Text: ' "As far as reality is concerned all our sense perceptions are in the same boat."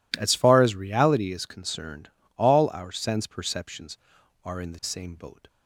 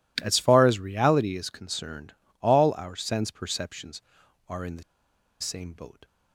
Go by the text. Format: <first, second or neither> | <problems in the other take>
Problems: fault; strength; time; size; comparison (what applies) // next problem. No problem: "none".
first | pauses between "concerned" and "all"; slight; at 2.1 s; 0.28 s long; slight in the first // pauses between "the" and "same"; noticeable; at 4.8 s; 0.58 s long